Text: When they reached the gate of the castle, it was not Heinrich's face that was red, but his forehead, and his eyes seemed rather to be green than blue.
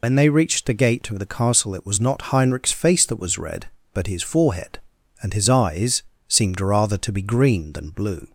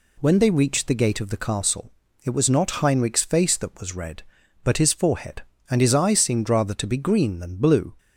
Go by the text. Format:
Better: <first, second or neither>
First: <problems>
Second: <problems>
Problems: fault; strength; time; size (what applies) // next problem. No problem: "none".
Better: second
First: loses the start of "When"; at 0.0 s; 85 ms // pauses between "eyes" and "seemed"; slight; at 6.0 s; 0.26 s long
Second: none